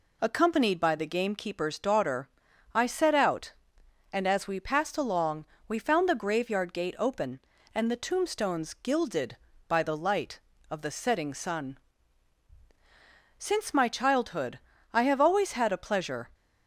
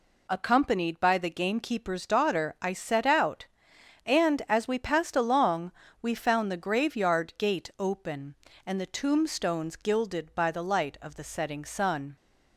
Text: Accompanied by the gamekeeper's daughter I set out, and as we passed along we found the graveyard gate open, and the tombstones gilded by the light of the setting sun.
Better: second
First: pauses between "daughter" and "I"; noticeable; at 2.2 s; 0.46 s long // pauses between "along" and "we"; slight; at 5.4 s; 0.24 s long // goes on to say "Since my childhood I have always had a pleasure"; strong; from 13.3 s on; 2.9 s long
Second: pauses between "along" and "we"; slight; at 5.7 s; 0.30 s long

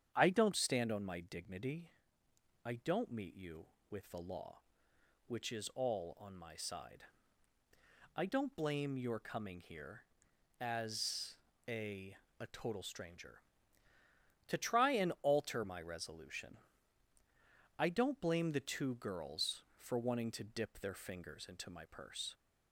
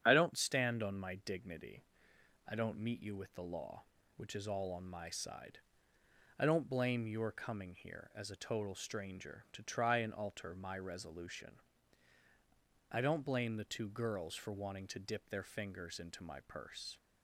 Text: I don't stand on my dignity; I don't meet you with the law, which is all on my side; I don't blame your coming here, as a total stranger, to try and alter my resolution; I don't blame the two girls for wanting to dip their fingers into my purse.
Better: second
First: starts louder than the rest; strong; until 1.1 s; 8.5 dB // pauses between "as" and "a"; slight; at 11.3 s; 0.32 s long // says "a" twice; at 12.4 s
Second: starts louder than the rest; strong; until 1.0 s; 8.5 dB

